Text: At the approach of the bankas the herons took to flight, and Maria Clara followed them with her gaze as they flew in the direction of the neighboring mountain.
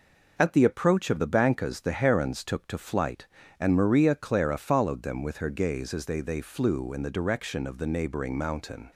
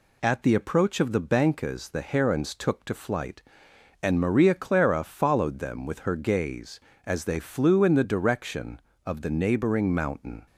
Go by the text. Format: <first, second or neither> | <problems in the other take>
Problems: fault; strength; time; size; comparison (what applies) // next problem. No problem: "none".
second | says "they" twice; at 6.2 s